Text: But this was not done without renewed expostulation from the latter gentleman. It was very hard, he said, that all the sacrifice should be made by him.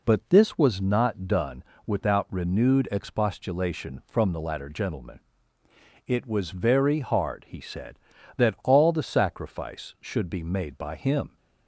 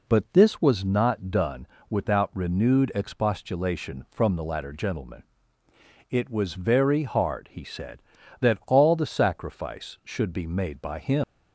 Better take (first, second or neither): first